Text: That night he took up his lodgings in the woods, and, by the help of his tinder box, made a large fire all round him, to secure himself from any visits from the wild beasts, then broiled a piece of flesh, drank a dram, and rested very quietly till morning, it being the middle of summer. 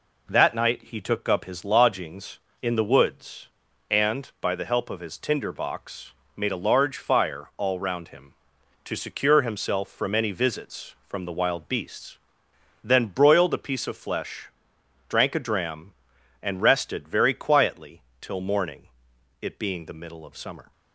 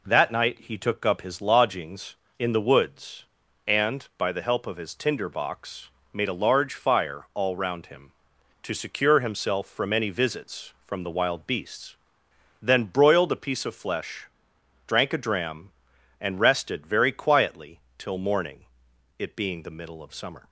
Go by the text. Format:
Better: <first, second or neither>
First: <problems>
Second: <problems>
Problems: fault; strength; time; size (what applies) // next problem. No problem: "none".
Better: neither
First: pauses between "quietly" and "till"; slight; at 18.0 s; 0.18 s long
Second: pauses between "quietly" and "till"; slight; at 17.7 s; 0.17 s long